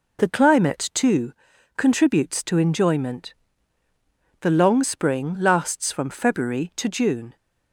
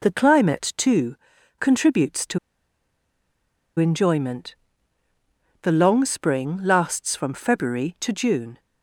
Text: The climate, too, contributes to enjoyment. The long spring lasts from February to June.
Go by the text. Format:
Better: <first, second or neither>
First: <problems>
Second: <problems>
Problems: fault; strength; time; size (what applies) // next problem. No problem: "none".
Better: first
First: none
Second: pauses between "to" and "enjoyment"; strong; at 2.3 s; 1.4 s long